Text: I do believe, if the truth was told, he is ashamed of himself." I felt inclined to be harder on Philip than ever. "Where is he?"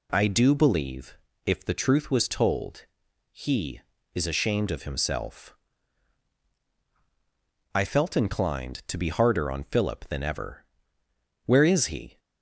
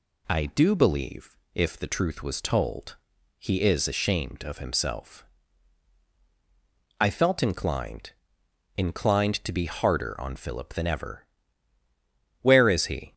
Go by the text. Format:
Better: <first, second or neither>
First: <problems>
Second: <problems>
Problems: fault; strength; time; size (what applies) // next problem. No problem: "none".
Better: first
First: none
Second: says "inclined" twice; at 8.7 s